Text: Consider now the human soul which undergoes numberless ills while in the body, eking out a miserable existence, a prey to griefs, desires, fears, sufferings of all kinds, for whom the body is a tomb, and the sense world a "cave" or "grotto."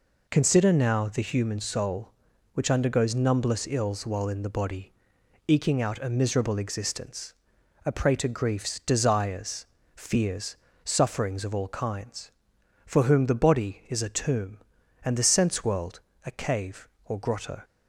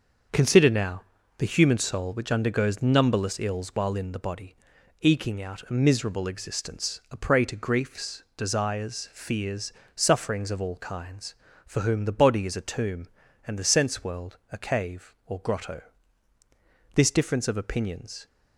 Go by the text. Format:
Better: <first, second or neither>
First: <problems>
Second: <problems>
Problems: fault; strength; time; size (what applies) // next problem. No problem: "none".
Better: first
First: pauses between "world" and "a"; slight; at 16.0 s; 0.24 s long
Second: starts louder than the rest; until 1.6 s; 6.5 dB // pauses between "now" and "the"; at 1.0 s; 0.38 s long // pauses between "world" and "a"; slight; at 14.3 s; 0.16 s long // goes on to say "This difference of opinions"; from 16.9 s on; 1.3 s long